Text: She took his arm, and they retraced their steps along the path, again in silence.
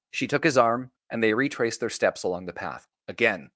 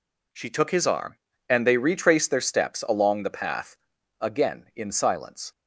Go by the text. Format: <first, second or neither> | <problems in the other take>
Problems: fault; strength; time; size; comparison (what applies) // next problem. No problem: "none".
second | stops before "in silence"; at 3.5 s